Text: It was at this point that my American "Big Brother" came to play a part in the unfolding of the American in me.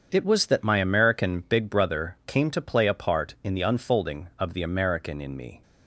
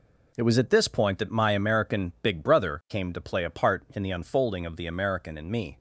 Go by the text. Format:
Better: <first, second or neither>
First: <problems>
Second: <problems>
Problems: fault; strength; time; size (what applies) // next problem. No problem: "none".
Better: second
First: starts louder than the rest; strong; until 1.1 s; 7.5 dB // skips "at this point"; at 0.4 s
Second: none